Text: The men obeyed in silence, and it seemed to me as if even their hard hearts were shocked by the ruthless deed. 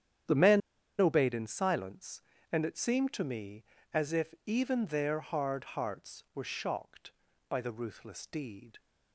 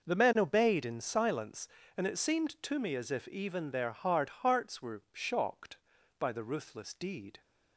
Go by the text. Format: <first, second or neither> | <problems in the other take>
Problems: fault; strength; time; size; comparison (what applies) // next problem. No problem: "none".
second | starts louder than the rest; strong; until 1.6 s; 9 dB // pauses between "men" and "obeyed"; at 0.6 s; 0.38 s long